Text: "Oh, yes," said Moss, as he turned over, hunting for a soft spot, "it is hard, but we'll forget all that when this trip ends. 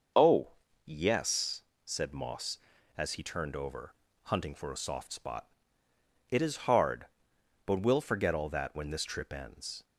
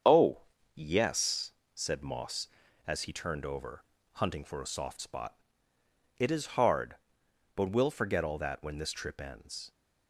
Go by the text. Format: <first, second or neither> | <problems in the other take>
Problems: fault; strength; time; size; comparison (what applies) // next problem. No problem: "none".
first | gets quieter; noticeable; throughout; 6 dB // starts louder than the rest; strong; until 1.3 s; 7.5 dB; noticeable in the first